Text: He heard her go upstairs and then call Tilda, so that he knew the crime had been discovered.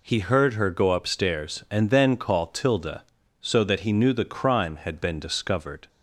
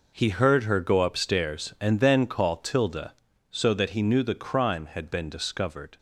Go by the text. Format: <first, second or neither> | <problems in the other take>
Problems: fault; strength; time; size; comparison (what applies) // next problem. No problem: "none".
first | gets quieter; strong; throughout; 12 dB